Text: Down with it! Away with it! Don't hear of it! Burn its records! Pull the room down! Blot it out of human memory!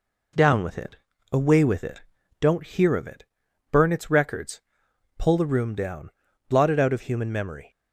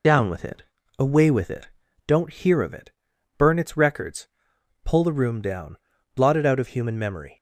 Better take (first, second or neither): first